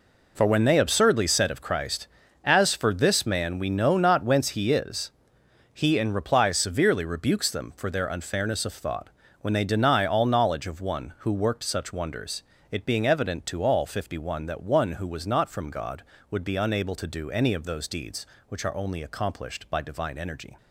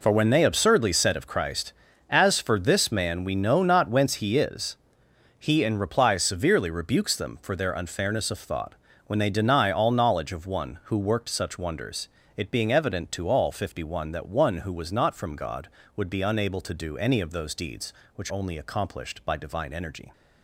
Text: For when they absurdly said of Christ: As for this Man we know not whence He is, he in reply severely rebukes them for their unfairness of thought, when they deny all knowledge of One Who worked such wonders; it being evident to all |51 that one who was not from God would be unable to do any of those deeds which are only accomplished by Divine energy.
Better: first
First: none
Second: skips "are"; at 18.3 s

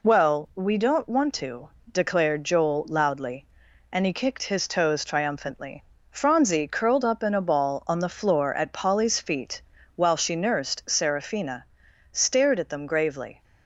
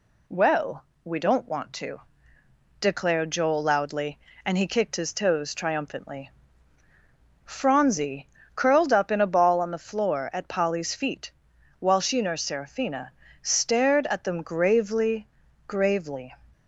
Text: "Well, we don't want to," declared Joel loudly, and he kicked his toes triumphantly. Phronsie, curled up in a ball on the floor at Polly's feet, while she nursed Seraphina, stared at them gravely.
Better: first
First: none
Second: says "gravely" twice; at 15.6 s

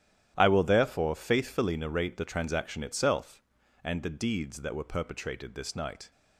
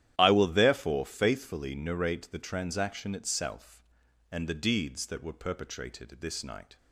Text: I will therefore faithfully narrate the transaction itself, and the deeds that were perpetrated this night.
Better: neither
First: starts louder than the rest; strong; until 1.3 s; 11.5 dB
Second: starts louder than the rest; strong; until 1.1 s; 11.5 dB

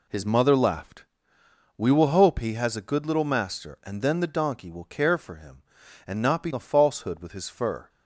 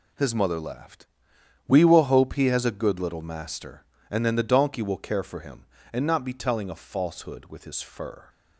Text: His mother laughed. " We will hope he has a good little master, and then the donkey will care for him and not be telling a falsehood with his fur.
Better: second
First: skips "telling"; at 6.5 s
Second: none

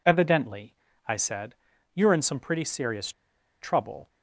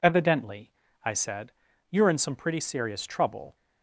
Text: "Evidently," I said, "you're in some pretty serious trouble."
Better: second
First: pauses between "serious" and "trouble"; noticeable; at 3.1 s; 0.51 s long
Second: none

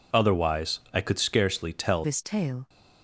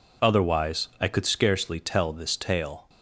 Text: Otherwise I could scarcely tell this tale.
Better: second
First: changes voice at "this"; from 2.0 s on; 0.6 s long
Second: none

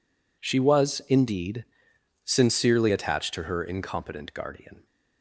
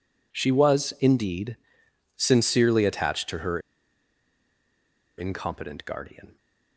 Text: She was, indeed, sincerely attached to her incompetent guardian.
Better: first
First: none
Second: pauses between "her" and "incompetent"; strong; at 3.5 s; 1.5 s long

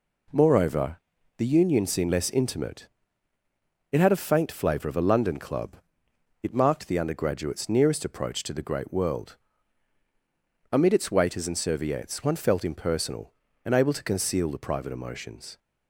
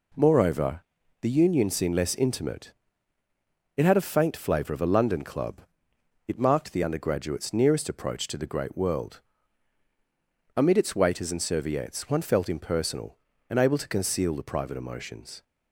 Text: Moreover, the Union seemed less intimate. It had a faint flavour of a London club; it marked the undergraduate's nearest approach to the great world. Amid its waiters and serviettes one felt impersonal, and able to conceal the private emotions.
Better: neither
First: none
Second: none

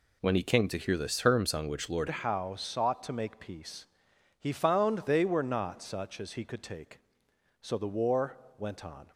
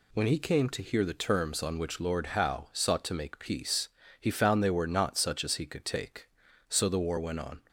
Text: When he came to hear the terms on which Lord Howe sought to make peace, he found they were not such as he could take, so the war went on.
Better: second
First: changes voice at "Howe"; from 2.0 s on; 7.1 s long // pauses between "war" and "went"; slight; at 8.3 s; 0.18 s long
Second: none

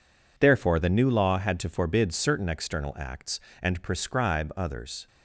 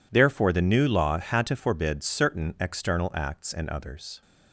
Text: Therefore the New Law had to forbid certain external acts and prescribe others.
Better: first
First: none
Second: skips "prescribe"; at 3.6 s

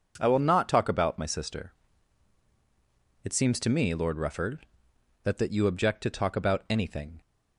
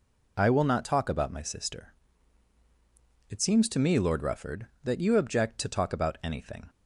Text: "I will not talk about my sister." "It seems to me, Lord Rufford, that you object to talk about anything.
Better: second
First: says "that" twice; at 5.3 s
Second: none

